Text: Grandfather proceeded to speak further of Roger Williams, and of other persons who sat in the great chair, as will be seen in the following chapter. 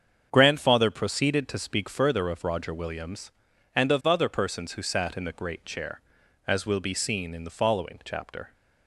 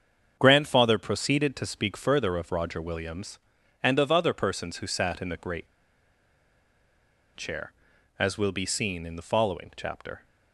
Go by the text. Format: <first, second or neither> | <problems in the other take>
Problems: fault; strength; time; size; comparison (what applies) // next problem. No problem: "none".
first | starts louder than the rest; strong; until 1.4 s; 7 dB; strong in the first // pauses between "great" and "chair"; strong; at 5.6 s; 1.6 s long